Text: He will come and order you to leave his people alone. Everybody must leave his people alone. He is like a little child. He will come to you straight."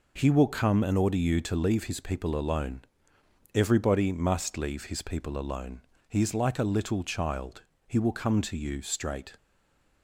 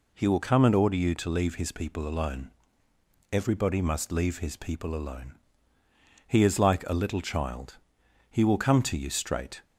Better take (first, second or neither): second